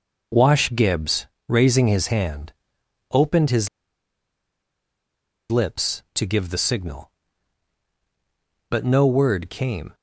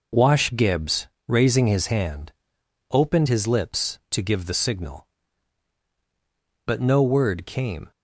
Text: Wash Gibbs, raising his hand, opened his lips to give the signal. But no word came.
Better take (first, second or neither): second